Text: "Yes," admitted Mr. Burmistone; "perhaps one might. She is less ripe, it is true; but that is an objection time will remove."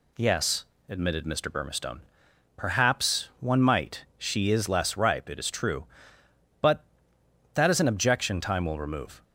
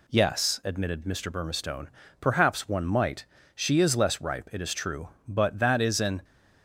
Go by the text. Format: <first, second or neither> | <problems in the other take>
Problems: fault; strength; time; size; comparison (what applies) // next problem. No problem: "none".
first | stops before "objection time will remove"; at 6.2 s